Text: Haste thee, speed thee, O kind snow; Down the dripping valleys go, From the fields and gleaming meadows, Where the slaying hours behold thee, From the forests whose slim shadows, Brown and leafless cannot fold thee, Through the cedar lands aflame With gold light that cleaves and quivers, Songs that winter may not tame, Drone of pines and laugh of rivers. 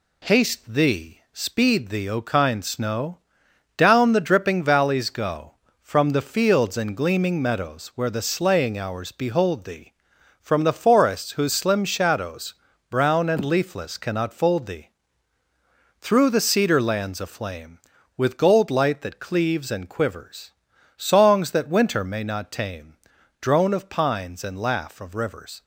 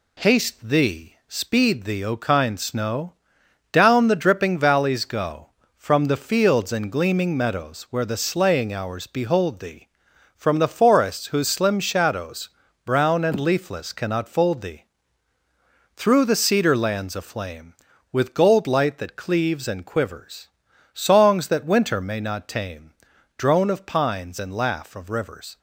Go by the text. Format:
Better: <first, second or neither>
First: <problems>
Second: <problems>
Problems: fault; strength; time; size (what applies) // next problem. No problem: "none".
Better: neither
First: none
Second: none